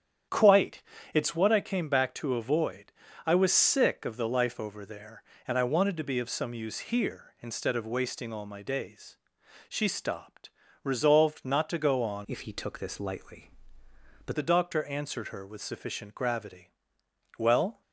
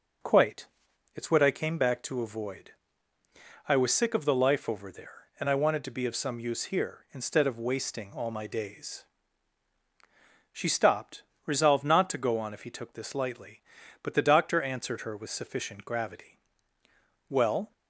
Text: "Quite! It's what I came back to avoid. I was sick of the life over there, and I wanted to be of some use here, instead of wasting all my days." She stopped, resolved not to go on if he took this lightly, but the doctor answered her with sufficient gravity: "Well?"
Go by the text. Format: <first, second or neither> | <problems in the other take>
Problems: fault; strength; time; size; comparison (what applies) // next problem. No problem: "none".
second | starts louder than the rest; strong; until 1.6 s; 9 dB // changes voice from "if" to "but"; from 12.2 to 14.3 s; 2.1 s long